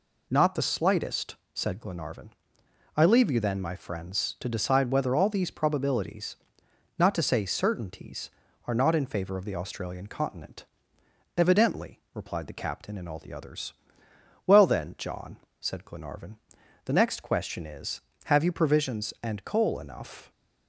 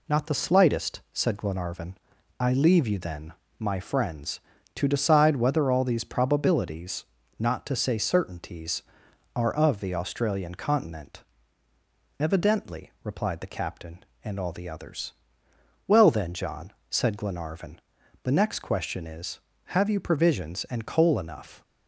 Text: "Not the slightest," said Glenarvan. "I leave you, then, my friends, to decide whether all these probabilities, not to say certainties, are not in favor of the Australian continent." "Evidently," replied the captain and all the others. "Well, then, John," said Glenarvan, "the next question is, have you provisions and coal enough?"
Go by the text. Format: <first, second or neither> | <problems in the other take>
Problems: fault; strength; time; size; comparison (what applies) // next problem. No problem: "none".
first | skips "not in favor"; at 9.5 s